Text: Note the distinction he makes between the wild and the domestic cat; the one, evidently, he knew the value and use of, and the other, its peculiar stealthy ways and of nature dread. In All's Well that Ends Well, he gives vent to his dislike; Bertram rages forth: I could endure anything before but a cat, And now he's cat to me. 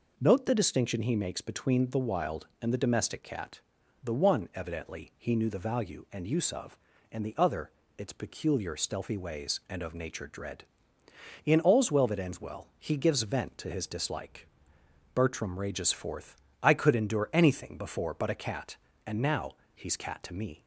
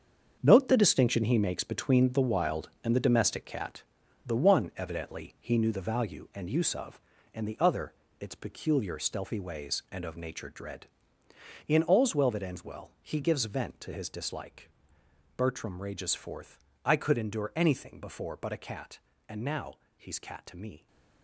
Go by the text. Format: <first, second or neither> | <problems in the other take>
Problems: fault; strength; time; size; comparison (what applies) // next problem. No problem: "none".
first | gets quieter; strong; throughout; 10 dB // pauses between "now" and "he's"; slight; at 19.7 s; 0.18 s long; slight in the first